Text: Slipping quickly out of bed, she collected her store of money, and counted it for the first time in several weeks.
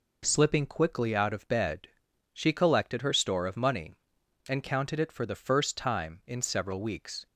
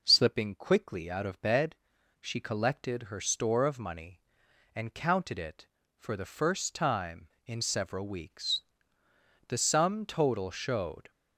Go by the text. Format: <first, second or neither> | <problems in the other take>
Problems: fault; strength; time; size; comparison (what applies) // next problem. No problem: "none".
first | goes on to say "The sum total showed"; from 9.4 s on; 1.6 s long